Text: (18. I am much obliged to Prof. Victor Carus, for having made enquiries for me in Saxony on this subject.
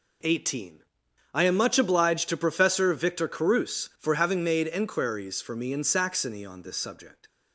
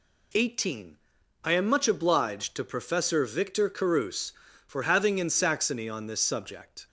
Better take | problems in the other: first | skips "made enquiries for me"; at 5.1 s

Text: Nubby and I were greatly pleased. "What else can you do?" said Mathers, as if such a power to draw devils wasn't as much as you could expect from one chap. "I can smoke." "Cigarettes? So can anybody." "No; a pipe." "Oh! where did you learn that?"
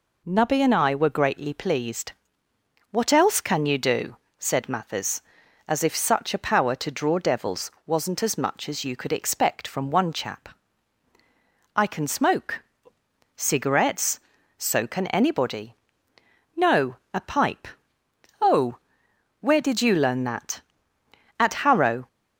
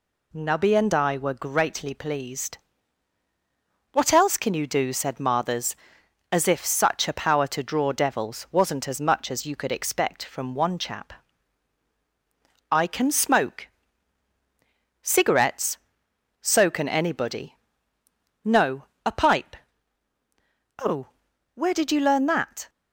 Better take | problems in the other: second | goes on to say "At Harrow"; noticeable; from 21.3 s on; 0.70 s long

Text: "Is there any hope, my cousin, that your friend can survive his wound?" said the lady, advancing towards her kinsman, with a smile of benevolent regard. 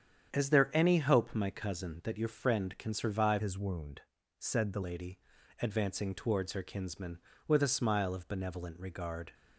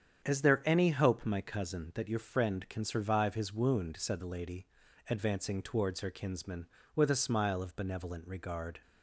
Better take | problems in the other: second | starts louder than the rest; strong; until 1.3 s; 8.5 dB; strong in the second // changes voice from "his" to "the"; from 3.3 to 4.8 s; 1.5 s long

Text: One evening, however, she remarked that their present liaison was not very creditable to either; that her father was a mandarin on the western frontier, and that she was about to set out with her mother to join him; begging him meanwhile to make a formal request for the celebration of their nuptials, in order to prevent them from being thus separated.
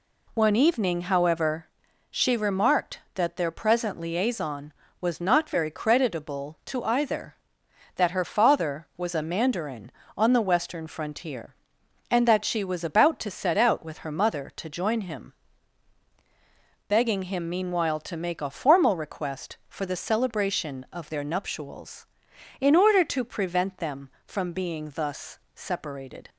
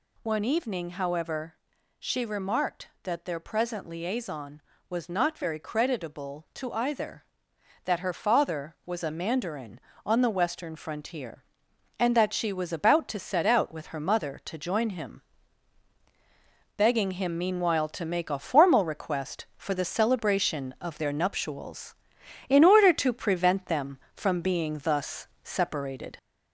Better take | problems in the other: first | gets louder; slight; throughout; 2.5 dB // pauses between "thus" and "separated"; slight; at 25.2 s; 0.16 s long; slight in the first

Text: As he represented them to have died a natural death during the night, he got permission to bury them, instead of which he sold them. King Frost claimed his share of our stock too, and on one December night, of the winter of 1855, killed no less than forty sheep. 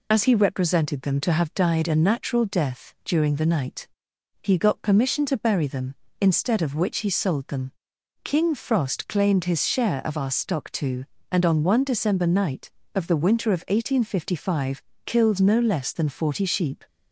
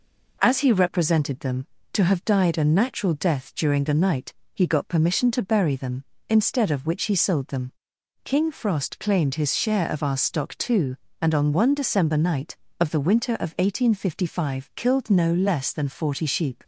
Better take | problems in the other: second | loses the start of "As"; at 0.1 s; 50 ms

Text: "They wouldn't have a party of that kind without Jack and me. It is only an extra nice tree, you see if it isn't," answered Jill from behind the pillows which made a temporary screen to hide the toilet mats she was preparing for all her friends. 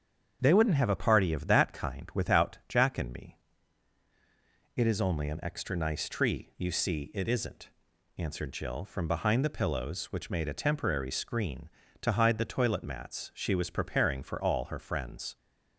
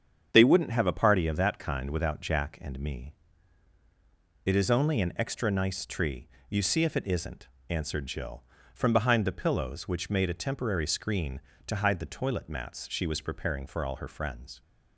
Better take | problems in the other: second | starts louder than the rest; strong; until 1.4 s; 7.5 dB; strong in the second // skips "if"; at 7.1 s

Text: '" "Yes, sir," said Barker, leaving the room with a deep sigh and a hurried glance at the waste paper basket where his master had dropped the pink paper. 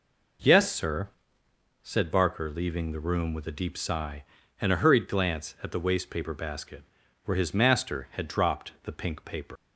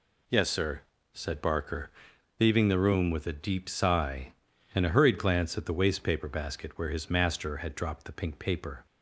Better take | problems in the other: second | pauses between "basket" and "where"; at 6.8 s; 0.42 s long // leaves "paper" unfinished; at 9.5 s; 110 ms

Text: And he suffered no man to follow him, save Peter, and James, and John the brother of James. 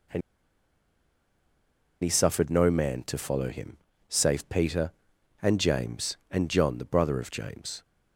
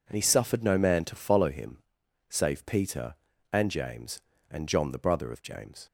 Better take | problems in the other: second | pauses between "And" and "he"; strong; at 0.2 s; 1.8 s long

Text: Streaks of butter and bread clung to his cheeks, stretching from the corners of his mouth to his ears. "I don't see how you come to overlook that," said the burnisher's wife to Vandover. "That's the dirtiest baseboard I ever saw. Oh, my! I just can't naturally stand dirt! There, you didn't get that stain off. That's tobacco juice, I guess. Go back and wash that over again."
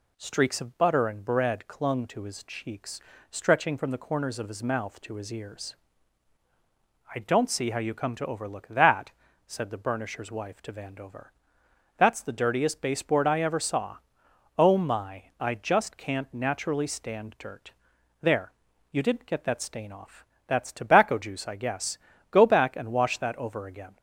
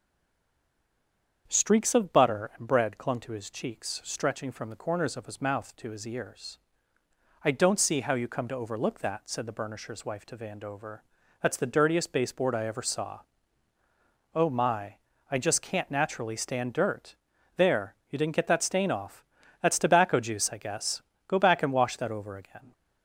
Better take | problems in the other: first | stays silent before the first word; noticeable; until 1.4 s; 1.4 s long // starts louder than the rest; strong; until 2.4 s; 7.5 dB

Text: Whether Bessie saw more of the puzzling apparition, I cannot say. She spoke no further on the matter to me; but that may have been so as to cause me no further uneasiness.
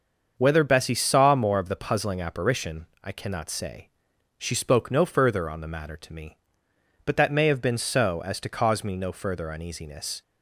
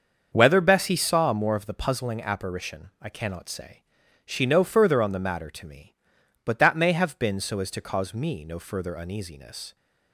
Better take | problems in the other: first | starts louder than the rest; until 1.3 s; 6.5 dB; also in the first // skips "spoke"; at 4.4 s

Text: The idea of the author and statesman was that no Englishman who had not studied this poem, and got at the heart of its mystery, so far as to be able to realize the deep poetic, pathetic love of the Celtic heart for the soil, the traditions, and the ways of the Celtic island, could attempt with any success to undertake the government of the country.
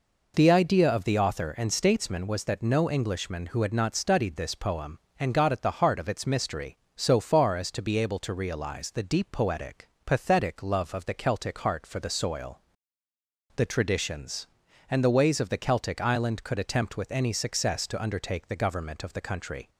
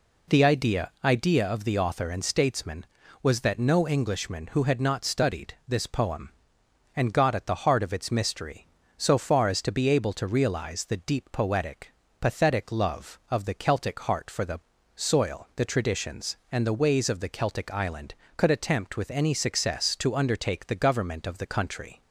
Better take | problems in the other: first | says "idea" twice; at 1.0 s // pauses between "the" and "soil"; slight; at 14.5 s; 0.36 s long

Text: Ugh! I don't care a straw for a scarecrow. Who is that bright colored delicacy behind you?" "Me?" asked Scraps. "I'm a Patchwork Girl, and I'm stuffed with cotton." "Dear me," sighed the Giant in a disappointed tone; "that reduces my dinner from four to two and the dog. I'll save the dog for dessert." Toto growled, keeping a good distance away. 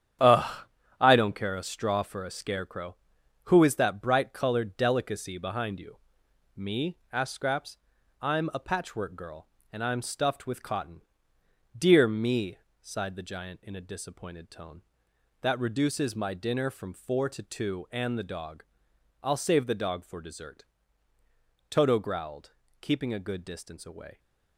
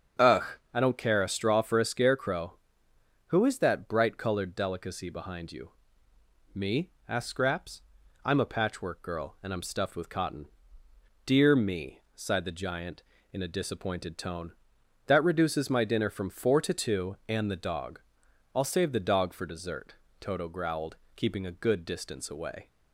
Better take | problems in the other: second | gets quieter; strong; throughout; 8.5 dB // starts louder than the rest; strong; until 1.6 s; 10 dB; strong in the second

